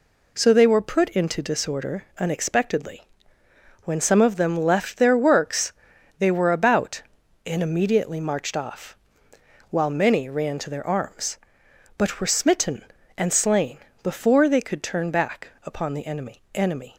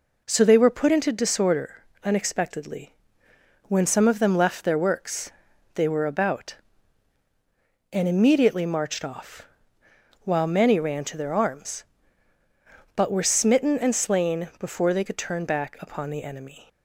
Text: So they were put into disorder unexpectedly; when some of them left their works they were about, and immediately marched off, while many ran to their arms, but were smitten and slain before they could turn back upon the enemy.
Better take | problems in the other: second | pauses between "disorder" and "unexpectedly"; slight; at 2.0 s; 0.16 s long; slight in the second // pauses between "works" and "they"; noticeable; at 5.7 s; 0.48 s long; also in the second // pauses between "slain" and "before"; slight; at 13.7 s; 0.24 s long // says "enemy" twice; at 16.5 s

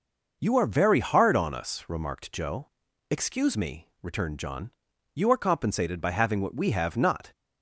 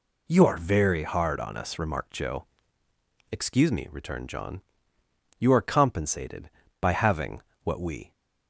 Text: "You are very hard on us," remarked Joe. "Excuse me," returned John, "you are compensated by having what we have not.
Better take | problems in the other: first | pauses between "having" and "what"; slight; at 7.4 s; 0.22 s long // stops before "have not"; at 8.1 s

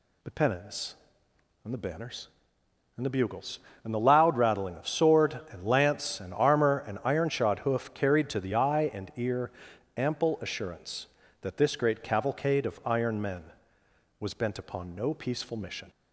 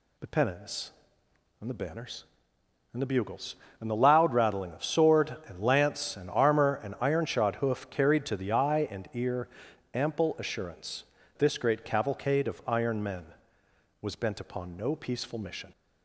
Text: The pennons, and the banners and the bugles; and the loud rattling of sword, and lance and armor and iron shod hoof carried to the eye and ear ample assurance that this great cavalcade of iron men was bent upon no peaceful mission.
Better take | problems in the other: first | pauses between "ear" and "ample"; noticeable; at 9.4 s; 0.46 s long; noticeable in the first // skips "that"; at 11.2 s

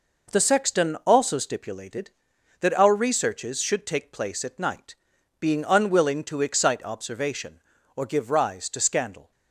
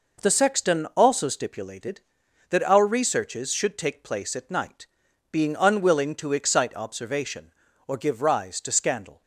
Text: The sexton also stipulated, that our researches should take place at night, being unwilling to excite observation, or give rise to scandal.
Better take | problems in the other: neither | none

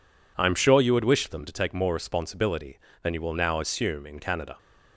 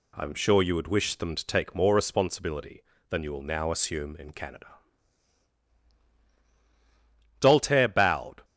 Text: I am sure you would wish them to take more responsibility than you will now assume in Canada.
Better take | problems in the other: first | goes on to say "Doltaire bowed"; noticeable; from 7.4 s on; 1.0 s long

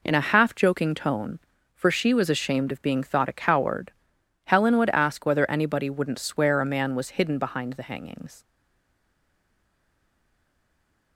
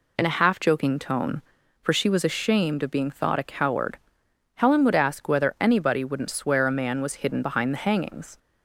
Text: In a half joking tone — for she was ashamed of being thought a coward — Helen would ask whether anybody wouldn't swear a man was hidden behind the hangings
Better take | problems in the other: second | stays silent after the last word; strong; from 8.4 s on; 2.7 s long

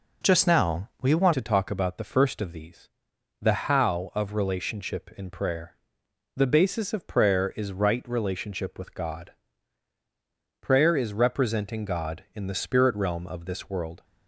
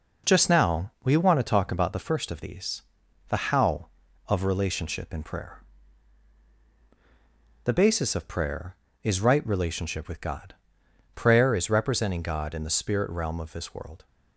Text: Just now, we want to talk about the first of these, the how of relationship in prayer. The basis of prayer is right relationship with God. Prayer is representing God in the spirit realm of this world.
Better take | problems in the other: second | changes voice at "to"; from 1.3 s on; 12.7 s long

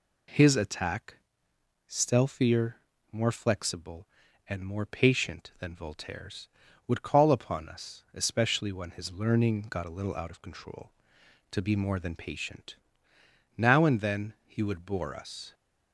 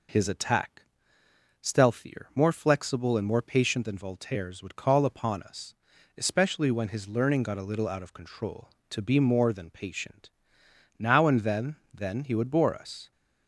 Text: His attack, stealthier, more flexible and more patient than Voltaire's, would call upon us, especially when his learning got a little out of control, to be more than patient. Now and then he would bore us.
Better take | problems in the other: first | says "then" twice; at 11.9 s

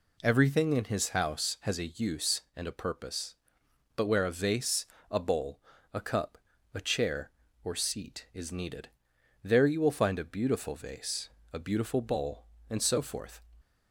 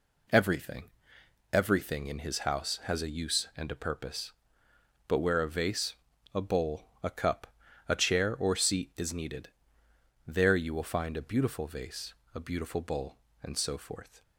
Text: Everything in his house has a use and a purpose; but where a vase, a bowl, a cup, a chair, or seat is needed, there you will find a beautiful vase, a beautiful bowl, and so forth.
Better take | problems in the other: first | says "Everything" twice; at 1.5 s

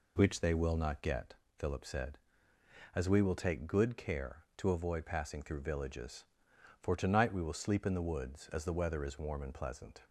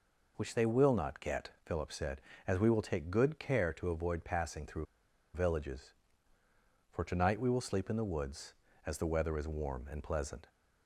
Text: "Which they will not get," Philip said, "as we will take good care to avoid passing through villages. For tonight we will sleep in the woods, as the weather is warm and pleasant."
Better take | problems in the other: first | pauses between "through" and "villages"; noticeable; at 4.8 s; 0.50 s long

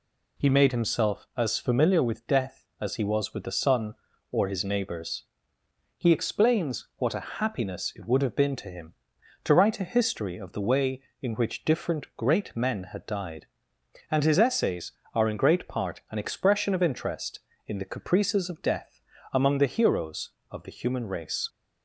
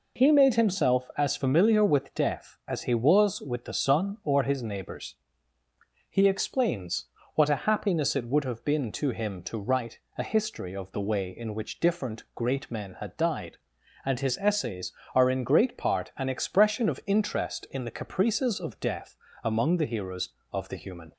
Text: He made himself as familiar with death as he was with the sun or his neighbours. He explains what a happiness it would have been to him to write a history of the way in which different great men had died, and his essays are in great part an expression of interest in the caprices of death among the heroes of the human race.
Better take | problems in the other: first | pauses between "explains" and "what"; slight; at 7.0 s; 0.30 s long // pauses between "write" and "a"; slight; at 9.9 s; 0.18 s long // pauses between "death" and "among"; slight; at 19.1 s; 0.28 s long; slight in the first // stops before "race"; at 21.1 s

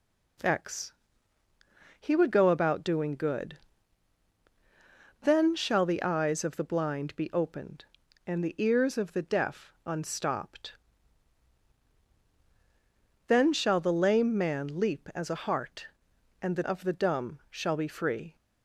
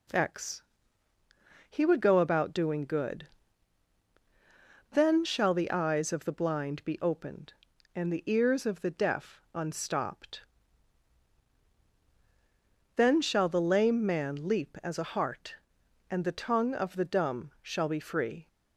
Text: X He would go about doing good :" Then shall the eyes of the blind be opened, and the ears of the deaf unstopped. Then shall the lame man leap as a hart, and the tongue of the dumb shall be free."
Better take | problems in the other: second | pauses between "X" and "He"; at 0.9 s; 1.0 s long; also in the second // skips "tongue"; at 16.6 s

